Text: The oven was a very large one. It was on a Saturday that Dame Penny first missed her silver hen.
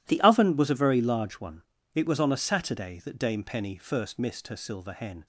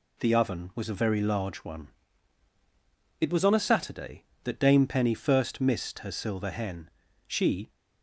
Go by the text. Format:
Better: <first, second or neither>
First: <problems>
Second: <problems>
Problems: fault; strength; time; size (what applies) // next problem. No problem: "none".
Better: first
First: none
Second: goes on to say "She"; slight; from 7.2 s on; 0.42 s long